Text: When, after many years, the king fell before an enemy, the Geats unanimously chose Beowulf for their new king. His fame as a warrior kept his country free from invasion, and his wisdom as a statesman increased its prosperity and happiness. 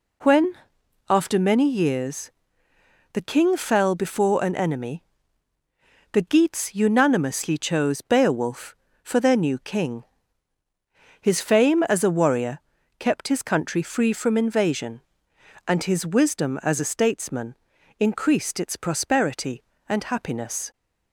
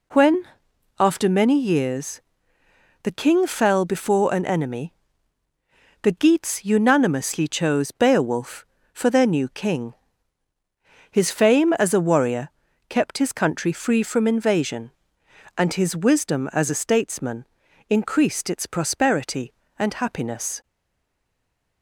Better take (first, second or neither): first